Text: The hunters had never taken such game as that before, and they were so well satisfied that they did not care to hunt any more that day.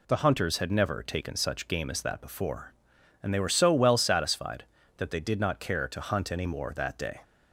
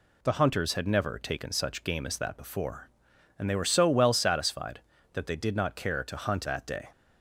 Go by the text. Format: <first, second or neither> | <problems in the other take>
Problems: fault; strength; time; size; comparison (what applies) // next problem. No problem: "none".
first | skips "any more"; at 6.4 s